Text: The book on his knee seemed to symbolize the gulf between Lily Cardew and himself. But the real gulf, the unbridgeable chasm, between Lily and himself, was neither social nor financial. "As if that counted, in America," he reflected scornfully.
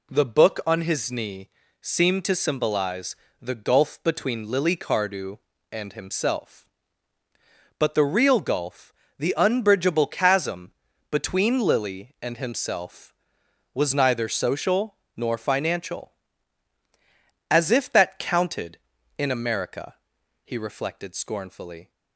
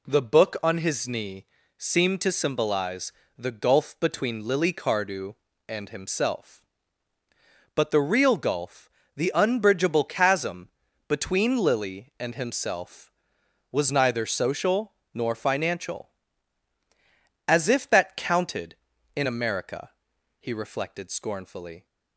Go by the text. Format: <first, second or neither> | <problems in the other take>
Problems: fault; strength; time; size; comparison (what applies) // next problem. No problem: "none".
neither | pauses between "knee" and "seemed"; slight; the same in both // pauses between "symbolize" and "the"; slight; the same in both // pauses between "social" and "nor"; slight; the same in both